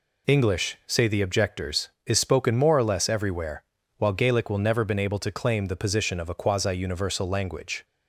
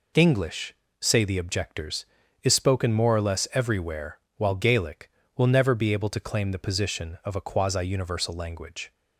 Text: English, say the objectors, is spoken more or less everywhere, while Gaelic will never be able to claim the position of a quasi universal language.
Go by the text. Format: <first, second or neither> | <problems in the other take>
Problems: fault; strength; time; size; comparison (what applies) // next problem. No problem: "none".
second | says "been" for "be"; at 4.8 s